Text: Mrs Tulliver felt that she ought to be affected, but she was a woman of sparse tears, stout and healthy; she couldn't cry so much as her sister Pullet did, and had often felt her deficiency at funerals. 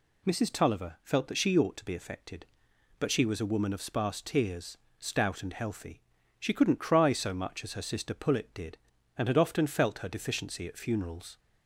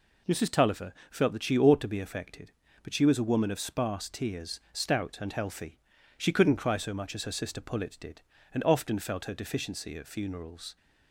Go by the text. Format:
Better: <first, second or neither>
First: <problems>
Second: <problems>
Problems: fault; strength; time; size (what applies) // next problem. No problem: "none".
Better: first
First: none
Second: pauses between "Tulliver" and "felt"; slight; at 0.9 s; 0.16 s long // skips "had"; at 8.6 s